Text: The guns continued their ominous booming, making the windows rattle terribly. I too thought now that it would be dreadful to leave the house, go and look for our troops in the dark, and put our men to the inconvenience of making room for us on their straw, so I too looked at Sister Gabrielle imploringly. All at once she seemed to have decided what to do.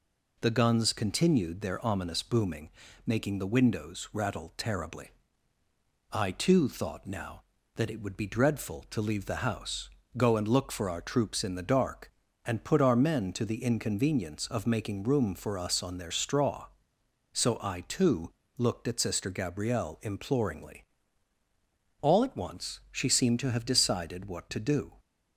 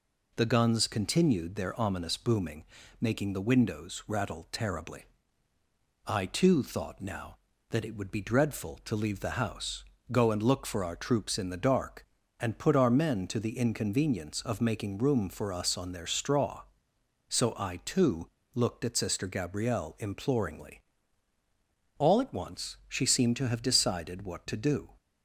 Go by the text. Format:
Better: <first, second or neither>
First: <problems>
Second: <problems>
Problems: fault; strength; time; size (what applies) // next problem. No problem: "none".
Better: neither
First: pauses between "too" and "looked"; slight; at 18.3 s; 0.26 s long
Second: pauses between "too" and "looked"; slight; at 18.2 s; 0.26 s long